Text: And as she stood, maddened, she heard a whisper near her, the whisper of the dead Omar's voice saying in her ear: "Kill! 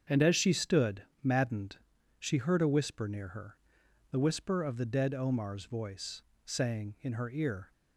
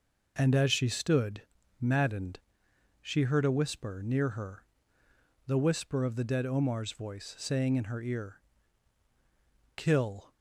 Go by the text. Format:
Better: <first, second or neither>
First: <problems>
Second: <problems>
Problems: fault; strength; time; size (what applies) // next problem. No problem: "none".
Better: second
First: starts louder than the rest; strong; until 1.2 s; 7 dB // pauses between "voice" and "saying"; slight; at 6.2 s; 0.24 s long // stops before "Kill"; at 7.7 s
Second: none